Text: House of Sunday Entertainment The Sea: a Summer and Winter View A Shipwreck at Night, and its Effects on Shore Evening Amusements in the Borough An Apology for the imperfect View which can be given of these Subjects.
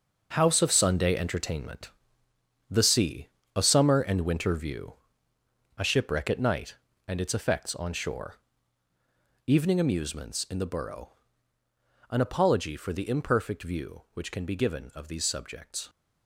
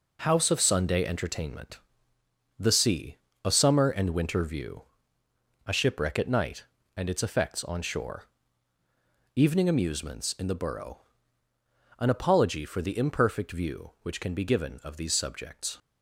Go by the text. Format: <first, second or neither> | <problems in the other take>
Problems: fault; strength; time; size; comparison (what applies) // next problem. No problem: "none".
second | gets quieter; strong; throughout; 9.5 dB // pauses between "Entertainment" and "The"; noticeable; at 1.8 s; 0.80 s long; noticeable in the second // pauses between "View" and "A"; noticeable; at 4.9 s; 0.84 s long; noticeable in the second // pauses between "Shore" and "Evening"; at 8.3 s; 1.1 s long; also in the second // pauses between "Borough" and "An"; at 11.0 s; 1.0 s long; also in the second